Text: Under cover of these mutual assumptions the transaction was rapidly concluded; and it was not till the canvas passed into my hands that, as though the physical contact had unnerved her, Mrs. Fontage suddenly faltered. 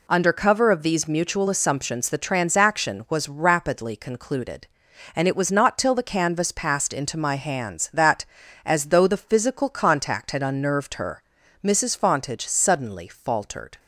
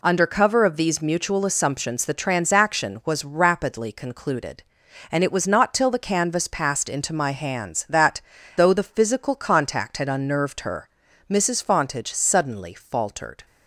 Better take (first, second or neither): first